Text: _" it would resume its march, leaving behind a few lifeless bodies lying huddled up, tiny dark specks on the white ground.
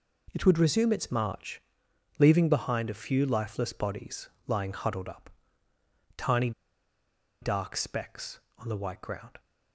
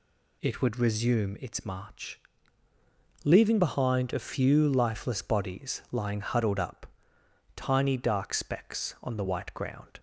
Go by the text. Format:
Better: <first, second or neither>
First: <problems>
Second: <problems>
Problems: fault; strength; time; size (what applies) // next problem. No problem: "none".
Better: second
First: pauses between "bodies" and "lying"; slight; at 4.2 s; 0.16 s long // pauses between "tiny" and "dark"; noticeable; at 6.5 s; 0.90 s long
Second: none